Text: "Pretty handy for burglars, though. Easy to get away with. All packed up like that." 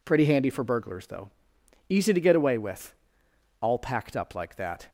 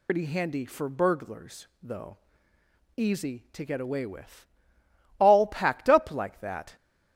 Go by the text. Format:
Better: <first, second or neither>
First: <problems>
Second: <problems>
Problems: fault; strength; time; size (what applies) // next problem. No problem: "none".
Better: first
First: none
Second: loses the start of "Pretty"; at 0.0 s; 125 ms